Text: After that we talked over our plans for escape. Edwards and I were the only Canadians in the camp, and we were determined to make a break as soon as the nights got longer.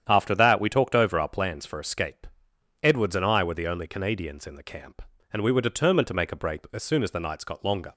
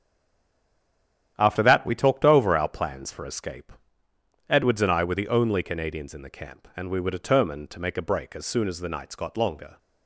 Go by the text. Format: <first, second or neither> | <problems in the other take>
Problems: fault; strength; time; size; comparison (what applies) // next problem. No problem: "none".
first | stays silent before the first word; noticeable; until 1.3 s; 1.3 s long // starts louder than the rest; strong; until 2.3 s; 10 dB; strong in the first